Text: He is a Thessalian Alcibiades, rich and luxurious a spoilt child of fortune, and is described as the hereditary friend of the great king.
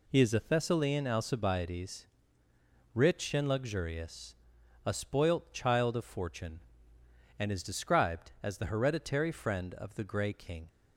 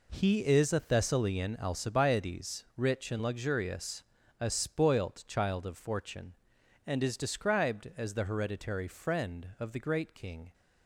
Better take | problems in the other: second | pauses between "luxurious" and "a"; noticeable; at 4.3 s; 0.52 s long; also in the second // says "grey" for "great"; at 10.0 s

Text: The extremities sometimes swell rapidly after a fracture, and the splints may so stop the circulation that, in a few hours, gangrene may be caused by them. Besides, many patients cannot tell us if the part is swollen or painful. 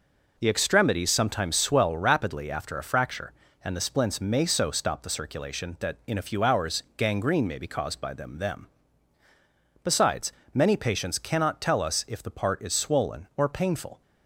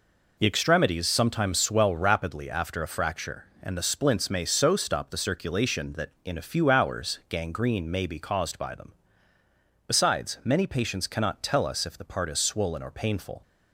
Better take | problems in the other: second | says "them" twice; at 8.3 s

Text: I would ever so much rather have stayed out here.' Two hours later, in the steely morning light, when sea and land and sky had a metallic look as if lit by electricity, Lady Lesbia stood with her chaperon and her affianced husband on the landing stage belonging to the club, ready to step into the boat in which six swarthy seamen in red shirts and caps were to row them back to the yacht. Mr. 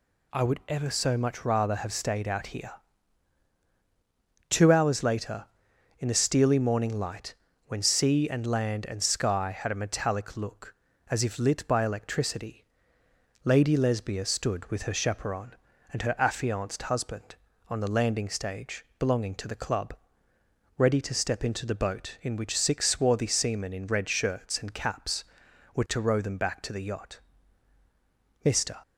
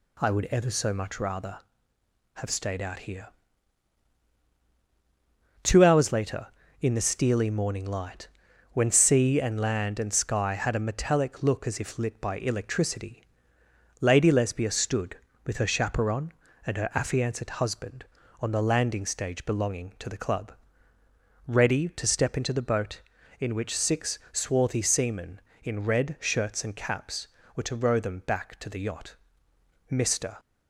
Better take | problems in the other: neither | none

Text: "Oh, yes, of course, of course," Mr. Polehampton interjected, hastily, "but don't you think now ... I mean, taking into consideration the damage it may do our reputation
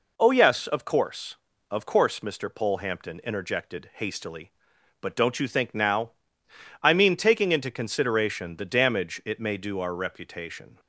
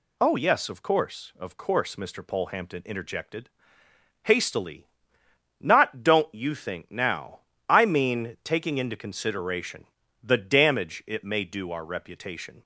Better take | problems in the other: first | says "not" for "but"; at 5.5 s // pauses between "consideration" and "the"; at 9.8 s; 0.40 s long

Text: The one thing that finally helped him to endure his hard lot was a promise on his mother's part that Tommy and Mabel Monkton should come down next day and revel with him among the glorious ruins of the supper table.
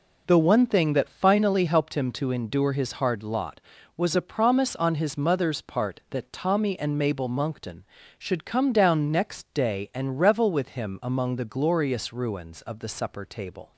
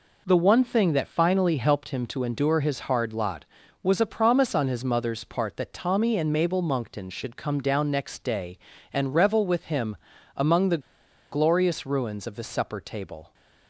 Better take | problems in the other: first | pauses between "him" and "among"; at 9.9 s; 0.38 s long // pauses between "the" and "glorious"; noticeable; at 10.8 s; 0.51 s long

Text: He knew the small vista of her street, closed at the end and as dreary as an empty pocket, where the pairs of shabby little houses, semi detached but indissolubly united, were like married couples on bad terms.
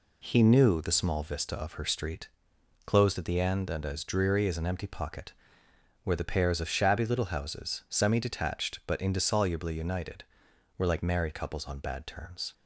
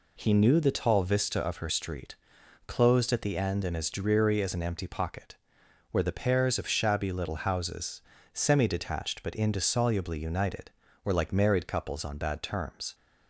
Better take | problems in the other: first | says "tall" for "small"; at 0.7 s

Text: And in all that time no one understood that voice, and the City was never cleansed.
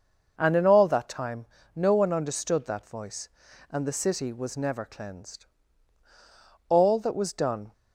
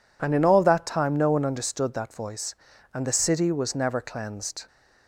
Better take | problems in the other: second | pauses between "time" and "no"; slight; at 1.4 s; 0.30 s long // goes on to say "All that was done"; noticeable; from 6.6 s on; 1.0 s long

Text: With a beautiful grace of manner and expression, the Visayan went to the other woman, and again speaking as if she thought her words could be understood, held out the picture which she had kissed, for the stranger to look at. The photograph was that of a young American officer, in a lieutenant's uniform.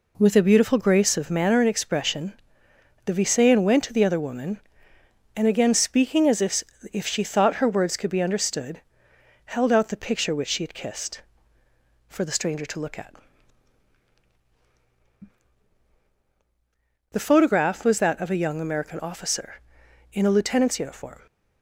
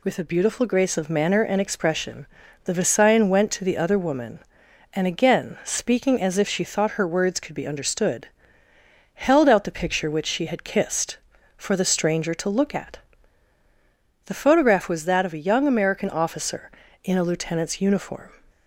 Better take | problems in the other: second | says "if" twice; at 6.8 s

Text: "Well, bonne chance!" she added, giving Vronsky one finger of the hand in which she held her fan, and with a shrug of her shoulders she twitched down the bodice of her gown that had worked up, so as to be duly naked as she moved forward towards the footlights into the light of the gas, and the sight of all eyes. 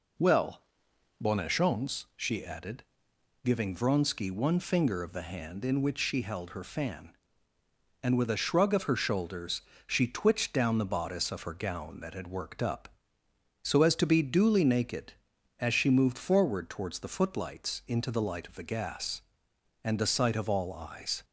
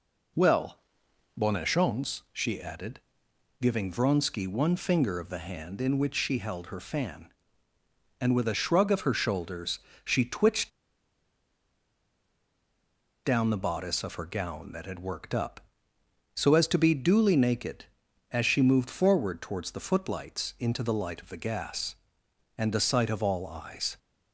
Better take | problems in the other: first | pauses between "shoulders" and "she"; slight; at 9.7 s; 0.26 s long; slight in the first // pauses between "twitched" and "down"; strong; at 10.7 s; 2.5 s long

